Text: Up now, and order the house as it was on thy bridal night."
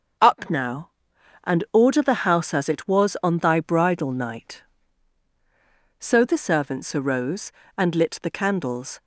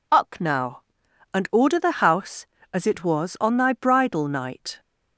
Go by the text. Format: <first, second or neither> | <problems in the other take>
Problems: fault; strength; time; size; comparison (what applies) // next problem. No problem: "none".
second | starts louder than the rest; until 1.8 s; 6.5 dB // goes on to say "So the servants arose and lit the candles"; strong; from 5.9 s on; 3.0 s long